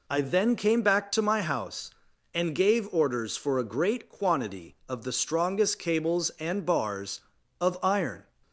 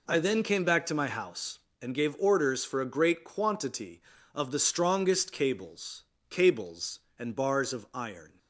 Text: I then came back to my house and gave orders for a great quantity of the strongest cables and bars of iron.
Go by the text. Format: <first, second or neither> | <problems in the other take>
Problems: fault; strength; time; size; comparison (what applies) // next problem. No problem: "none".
first | says "cables" twice; at 6.2 s